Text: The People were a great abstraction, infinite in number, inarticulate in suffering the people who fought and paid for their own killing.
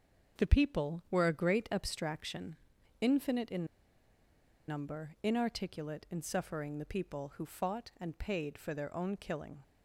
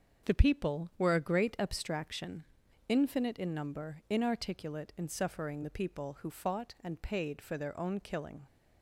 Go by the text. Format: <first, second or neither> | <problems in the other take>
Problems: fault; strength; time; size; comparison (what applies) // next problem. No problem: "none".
second | starts louder than the rest; until 1.4 s; 6.5 dB; also in the second // pauses between "in" and "number"; at 3.6 s; 1.0 s long